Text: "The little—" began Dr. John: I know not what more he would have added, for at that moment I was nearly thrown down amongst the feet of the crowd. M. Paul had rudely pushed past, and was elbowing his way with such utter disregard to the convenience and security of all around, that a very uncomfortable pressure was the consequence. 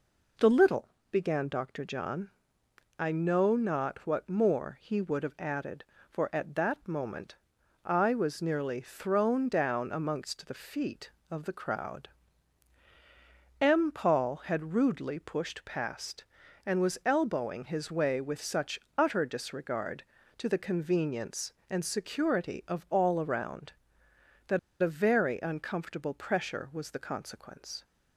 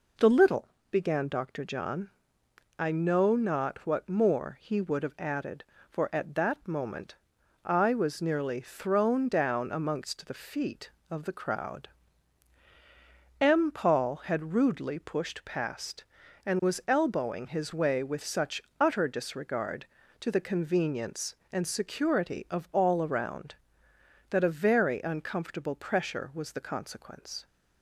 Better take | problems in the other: second | pauses between "moment" and "I"; noticeable; at 7.3 s; 0.50 s long; noticeable in the second // pauses between "such" and "utter"; slight; at 18.7 s; 0.16 s long; slight in the second // pauses between "that" and "a"; slight; at 24.5 s; 0.22 s long

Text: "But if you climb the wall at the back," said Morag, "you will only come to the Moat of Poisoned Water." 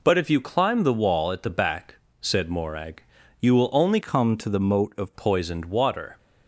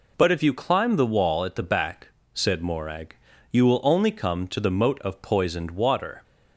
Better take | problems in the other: second | changes voice from "come" to "of"; from 4.0 to 5.1 s; 1.1 s long

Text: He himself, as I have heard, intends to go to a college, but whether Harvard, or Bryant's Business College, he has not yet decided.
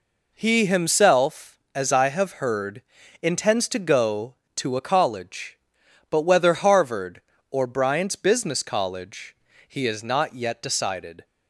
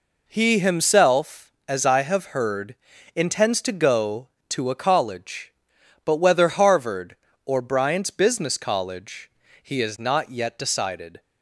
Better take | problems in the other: neither | none

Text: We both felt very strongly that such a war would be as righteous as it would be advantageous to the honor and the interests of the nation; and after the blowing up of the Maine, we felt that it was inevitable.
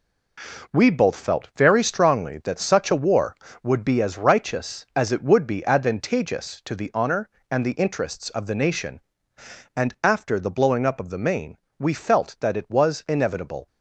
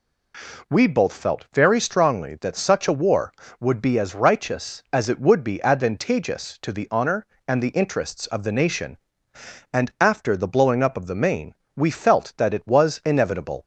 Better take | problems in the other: second | gets quieter; strong; throughout; 8.5 dB

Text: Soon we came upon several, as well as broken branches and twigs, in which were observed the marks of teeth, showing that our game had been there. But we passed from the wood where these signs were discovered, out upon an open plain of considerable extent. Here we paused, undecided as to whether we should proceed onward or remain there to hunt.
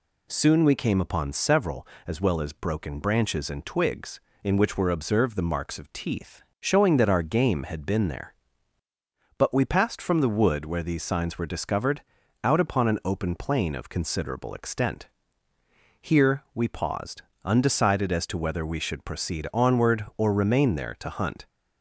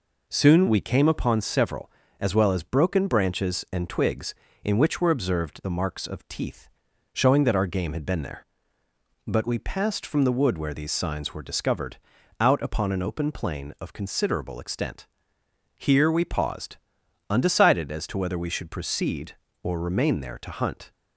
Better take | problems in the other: first | skips "onward"; at 19.4 s

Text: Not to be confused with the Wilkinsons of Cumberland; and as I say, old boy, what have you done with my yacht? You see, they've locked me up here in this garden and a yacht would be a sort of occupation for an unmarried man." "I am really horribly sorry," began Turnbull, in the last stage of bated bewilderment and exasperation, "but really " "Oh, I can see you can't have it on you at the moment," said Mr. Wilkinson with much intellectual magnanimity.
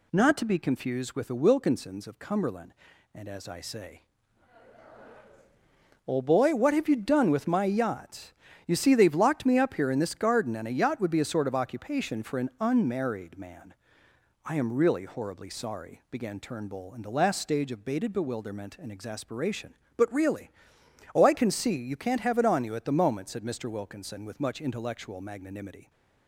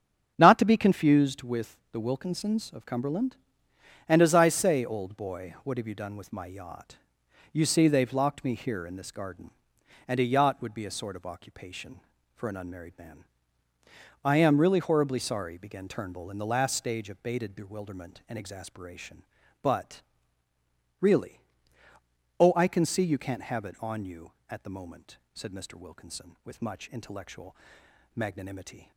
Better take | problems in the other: first | starts louder than the rest; strong; until 1.3 s; 8 dB // pauses between "with" and "the"; slight; at 1.7 s; 0.16 s long // skips "up"; at 8.5 s // pauses between "but" and "really"; noticeable; at 20.0 s; 0.98 s long // pauses between "intellectual" and "magnanimity"; noticeable; at 27.5 s; 0.62 s long

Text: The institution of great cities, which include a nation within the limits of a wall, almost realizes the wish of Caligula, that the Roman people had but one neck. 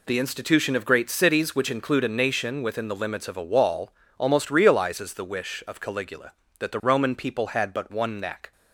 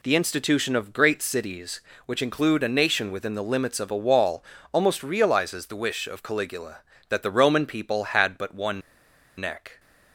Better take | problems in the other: first | pauses between "one" and "neck"; noticeable; at 8.8 s; 0.58 s long

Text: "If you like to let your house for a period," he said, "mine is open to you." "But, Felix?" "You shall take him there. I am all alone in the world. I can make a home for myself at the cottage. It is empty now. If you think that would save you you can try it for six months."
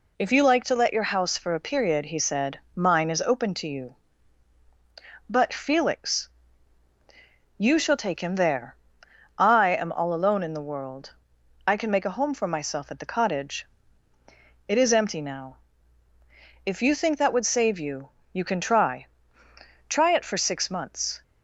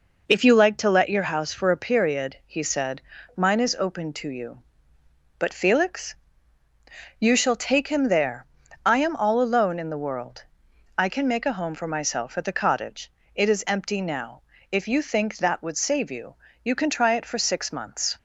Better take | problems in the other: second | pauses between "you" and "you"; slight; at 18.0 s; 0.22 s long; slight in the second // says "try" twice; at 19.8 s

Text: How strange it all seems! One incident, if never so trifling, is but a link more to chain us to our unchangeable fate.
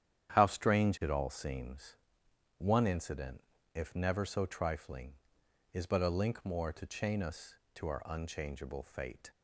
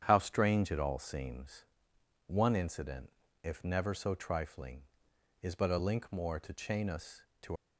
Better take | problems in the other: first | starts louder than the rest; strong; until 1.0 s; 8.5 dB; strong in the first // stops before "our unchangeable fate"; at 7.5 s

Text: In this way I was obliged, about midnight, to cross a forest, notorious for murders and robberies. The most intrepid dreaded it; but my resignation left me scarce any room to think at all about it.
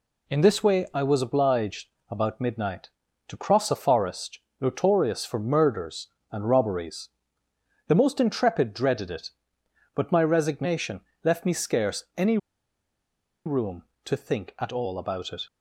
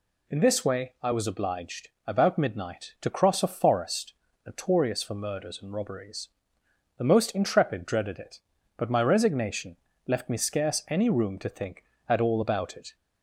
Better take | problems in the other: second | pauses between "resignation" and "left"; slight; at 10.9 s; 0.24 s long; slight in the second // pauses between "any" and "room"; at 12.3 s; 1.0 s long

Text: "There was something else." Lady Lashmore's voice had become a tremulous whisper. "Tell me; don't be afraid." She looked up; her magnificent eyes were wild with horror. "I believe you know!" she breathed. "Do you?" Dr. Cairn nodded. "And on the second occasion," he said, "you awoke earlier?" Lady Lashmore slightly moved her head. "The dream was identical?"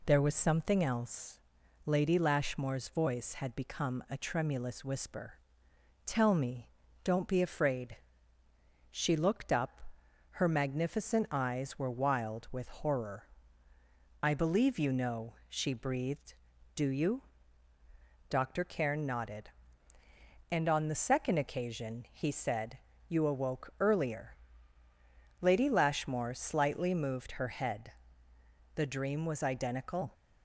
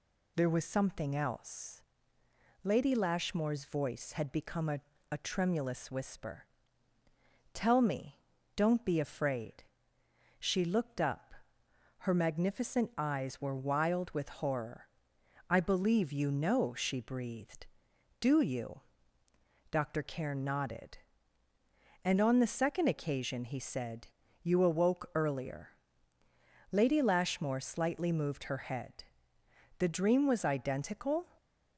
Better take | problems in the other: first | says "a" twice; at 5.1 s

